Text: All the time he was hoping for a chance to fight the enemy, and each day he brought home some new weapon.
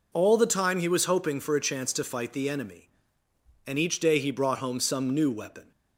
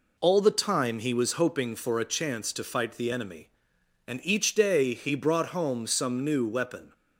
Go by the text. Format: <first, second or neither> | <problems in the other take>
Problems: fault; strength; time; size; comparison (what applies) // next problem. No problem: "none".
neither | none